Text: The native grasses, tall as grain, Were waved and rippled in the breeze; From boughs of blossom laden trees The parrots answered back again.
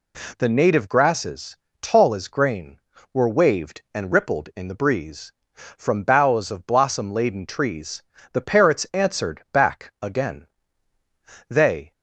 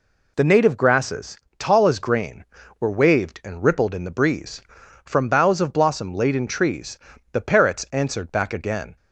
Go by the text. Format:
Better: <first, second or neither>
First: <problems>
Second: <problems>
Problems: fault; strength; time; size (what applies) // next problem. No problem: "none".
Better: second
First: pauses between "trees" and "The"; slight; at 8.0 s; 0.30 s long // goes on to say "They"; slight; from 11.4 s on; 0.42 s long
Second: pauses between "trees" and "The"; slight; at 6.9 s; 0.36 s long